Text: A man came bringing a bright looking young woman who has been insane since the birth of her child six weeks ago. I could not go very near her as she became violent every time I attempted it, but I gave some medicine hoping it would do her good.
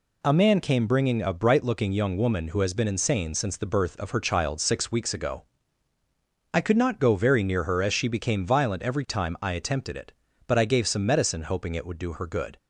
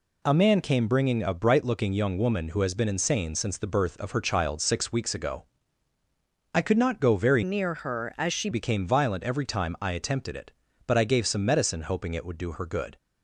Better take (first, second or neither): first